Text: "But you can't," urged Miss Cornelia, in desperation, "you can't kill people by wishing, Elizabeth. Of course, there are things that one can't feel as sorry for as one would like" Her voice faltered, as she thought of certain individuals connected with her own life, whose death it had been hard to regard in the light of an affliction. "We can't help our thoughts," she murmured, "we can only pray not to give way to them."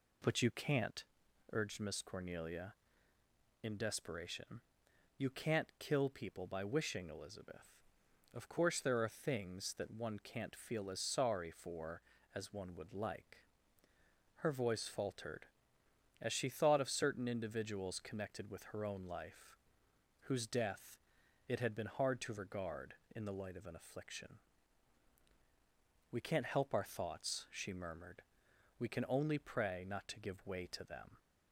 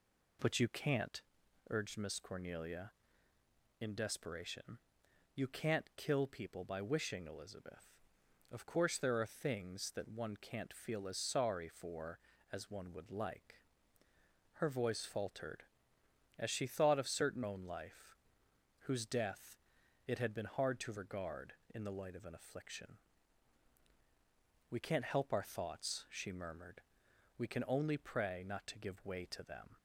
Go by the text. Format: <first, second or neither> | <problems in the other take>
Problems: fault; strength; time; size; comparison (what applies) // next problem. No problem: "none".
first | pauses between "like" and "Her"; noticeable; at 13.6 s; 0.94 s long; noticeable in the first // skips "individuals connected with her"; at 17.4 s // pauses between "death" and "it"; noticeable; at 19.5 s; 0.48 s long; noticeable in the first